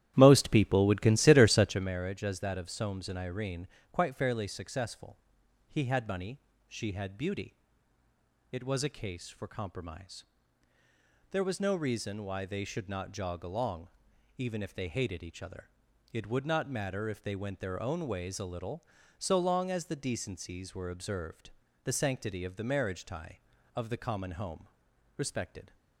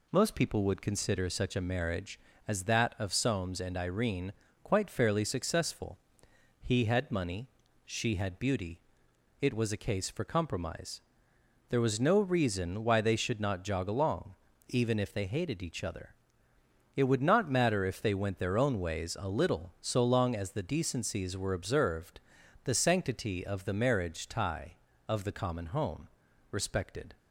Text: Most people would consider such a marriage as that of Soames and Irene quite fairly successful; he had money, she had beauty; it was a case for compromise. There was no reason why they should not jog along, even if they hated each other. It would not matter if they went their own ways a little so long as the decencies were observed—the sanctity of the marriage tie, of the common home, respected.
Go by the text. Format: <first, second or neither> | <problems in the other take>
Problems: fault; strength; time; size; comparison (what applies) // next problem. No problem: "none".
second | starts louder than the rest; strong; until 1.9 s; 12.5 dB // pauses between "Irene" and "quite"; slight; at 3.6 s; 0.26 s long; slight in the second